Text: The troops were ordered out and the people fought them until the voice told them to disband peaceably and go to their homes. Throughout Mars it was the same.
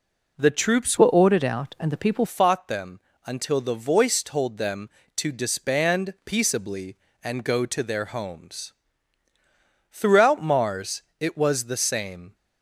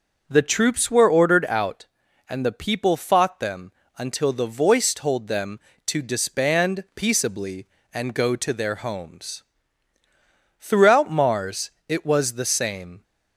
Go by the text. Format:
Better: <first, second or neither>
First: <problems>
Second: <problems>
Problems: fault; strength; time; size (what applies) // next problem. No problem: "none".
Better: second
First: changes voice from "were" to "people"; from 0.9 to 2.2 s; 1.3 s long // pauses between "them" and "until"; slight; at 2.9 s; 0.26 s long // pauses between "Mars" and "it"; slight; at 11.0 s; 0.18 s long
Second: pauses between "them" and "until"; slight; at 3.7 s; 0.26 s long // pauses between "Mars" and "it"; slight; at 11.7 s; 0.18 s long